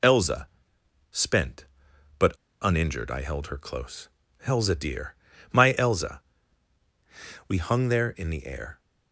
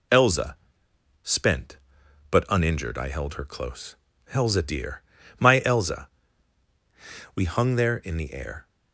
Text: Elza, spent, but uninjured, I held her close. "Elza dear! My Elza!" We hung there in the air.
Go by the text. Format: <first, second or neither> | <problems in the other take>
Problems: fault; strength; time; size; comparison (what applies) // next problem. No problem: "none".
second | pauses between "but" and "uninjured"; slight; at 2.3 s; 0.28 s long